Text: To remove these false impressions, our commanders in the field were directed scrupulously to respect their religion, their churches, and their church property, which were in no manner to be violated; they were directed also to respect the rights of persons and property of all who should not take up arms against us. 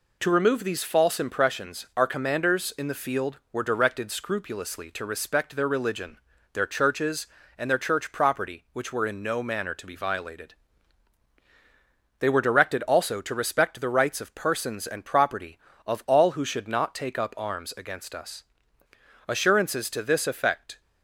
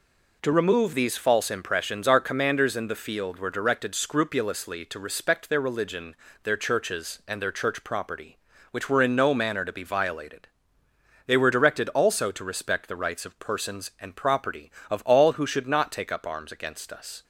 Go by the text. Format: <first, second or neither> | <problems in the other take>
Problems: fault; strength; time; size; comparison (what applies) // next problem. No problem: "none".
second | goes on to say "Assurances to this effect"; from 19.2 s on; 1.5 s long